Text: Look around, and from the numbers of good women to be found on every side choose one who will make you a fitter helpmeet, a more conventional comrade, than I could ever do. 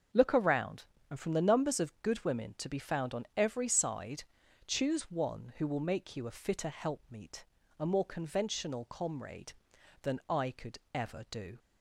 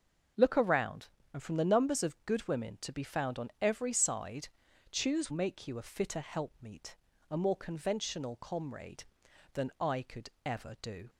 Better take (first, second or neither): first